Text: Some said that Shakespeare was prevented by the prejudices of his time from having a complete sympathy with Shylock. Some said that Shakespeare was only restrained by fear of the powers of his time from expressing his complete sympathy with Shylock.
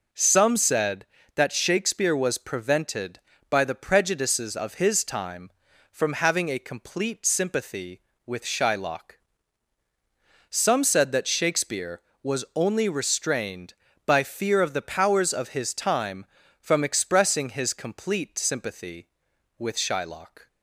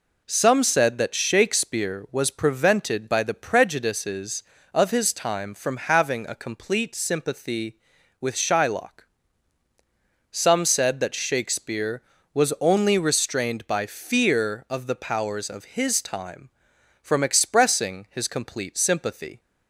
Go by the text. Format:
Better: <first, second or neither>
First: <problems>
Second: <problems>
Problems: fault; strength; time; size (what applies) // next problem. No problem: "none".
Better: first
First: none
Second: stops before "with Shylock"; at 19.3 s